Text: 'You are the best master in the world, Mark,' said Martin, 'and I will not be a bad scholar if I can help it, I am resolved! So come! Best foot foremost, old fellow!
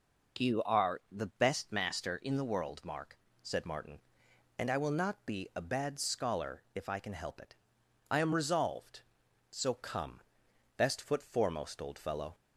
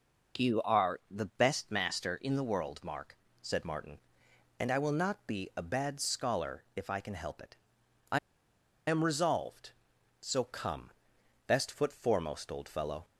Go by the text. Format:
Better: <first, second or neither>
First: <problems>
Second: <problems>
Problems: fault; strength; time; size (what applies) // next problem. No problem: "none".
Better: first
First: none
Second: pauses between "I" and "am"; noticeable; at 8.1 s; 0.69 s long